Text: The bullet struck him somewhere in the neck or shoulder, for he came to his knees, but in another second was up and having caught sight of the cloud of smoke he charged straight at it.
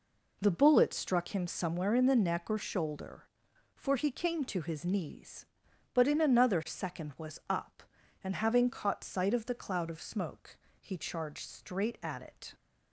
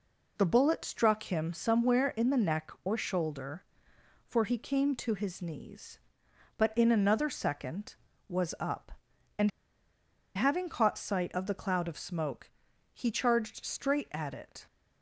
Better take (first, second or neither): first